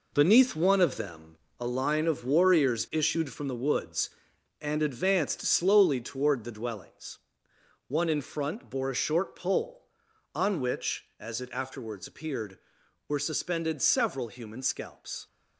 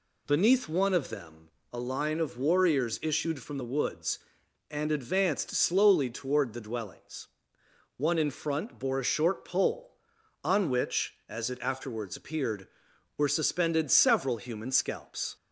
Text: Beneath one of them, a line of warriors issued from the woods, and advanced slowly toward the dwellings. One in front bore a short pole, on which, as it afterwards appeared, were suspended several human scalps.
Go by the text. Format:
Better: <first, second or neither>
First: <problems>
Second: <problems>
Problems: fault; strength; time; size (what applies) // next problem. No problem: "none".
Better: second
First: gets quieter; strong; throughout; 7.5 dB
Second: none